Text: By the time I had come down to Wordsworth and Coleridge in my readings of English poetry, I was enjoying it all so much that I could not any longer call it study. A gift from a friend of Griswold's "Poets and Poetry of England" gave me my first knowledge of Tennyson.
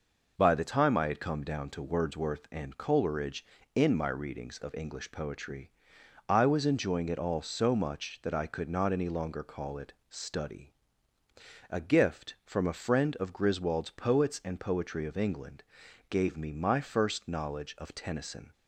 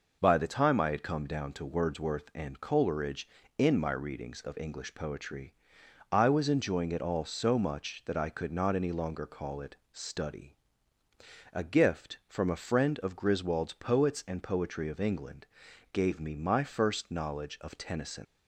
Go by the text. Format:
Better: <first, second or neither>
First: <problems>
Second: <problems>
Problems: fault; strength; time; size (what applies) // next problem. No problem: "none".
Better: first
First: pauses between "it" and "study"; slight; at 9.9 s; 0.16 s long // pauses between "England" and "gave"; noticeable; at 15.6 s; 0.46 s long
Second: pauses between "it" and "study"; slight; at 9.7 s; 0.16 s long // pauses between "England" and "gave"; noticeable; at 15.4 s; 0.46 s long // leaves "Tennyson" unfinished; at 18.2 s; 95 ms